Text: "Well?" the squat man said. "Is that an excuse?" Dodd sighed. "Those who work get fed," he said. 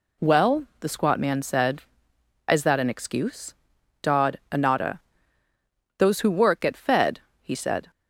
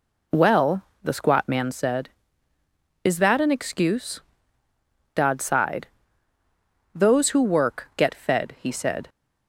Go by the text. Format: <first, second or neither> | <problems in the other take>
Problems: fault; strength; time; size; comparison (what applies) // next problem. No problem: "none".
second | says "anata" for "sighed"; at 4.5 s